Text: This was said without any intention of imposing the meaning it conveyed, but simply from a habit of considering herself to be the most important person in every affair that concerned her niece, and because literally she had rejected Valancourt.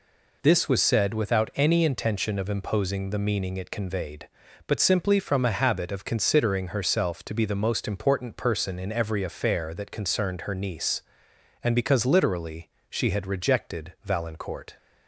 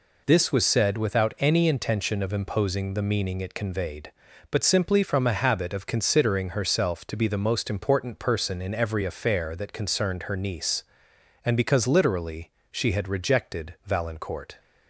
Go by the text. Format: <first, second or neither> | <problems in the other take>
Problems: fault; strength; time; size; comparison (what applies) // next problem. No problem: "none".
neither | pauses between "literally" and "she"; slight; the same in both